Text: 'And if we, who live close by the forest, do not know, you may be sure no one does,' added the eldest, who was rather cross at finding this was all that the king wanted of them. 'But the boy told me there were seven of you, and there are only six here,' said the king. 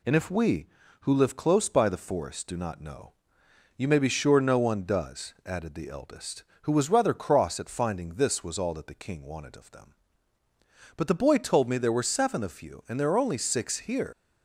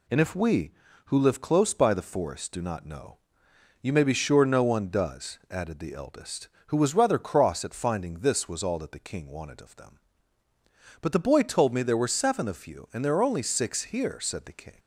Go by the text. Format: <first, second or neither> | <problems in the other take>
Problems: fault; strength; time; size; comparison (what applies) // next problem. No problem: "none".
second | stops before "said the king"; at 14.1 s